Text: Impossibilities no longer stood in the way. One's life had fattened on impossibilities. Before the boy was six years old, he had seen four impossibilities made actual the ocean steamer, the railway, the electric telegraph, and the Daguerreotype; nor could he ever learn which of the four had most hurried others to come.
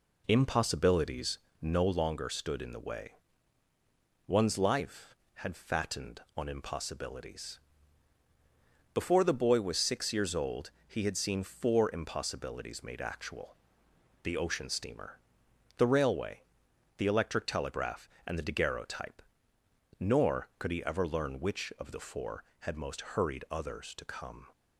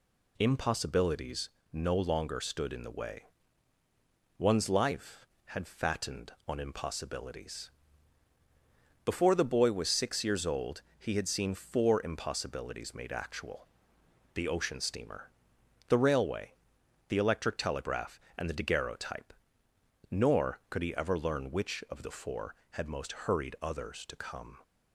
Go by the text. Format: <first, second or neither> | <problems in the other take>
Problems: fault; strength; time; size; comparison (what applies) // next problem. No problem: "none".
second | starts louder than the rest; slight; until 2.1 s; 3.5 dB // pauses between "Impossibilities" and "no"; slight; at 1.3 s; 0.24 s long; slight in the second // pauses between "actual" and "the"; noticeable; at 13.5 s; 0.68 s long; noticeable in the second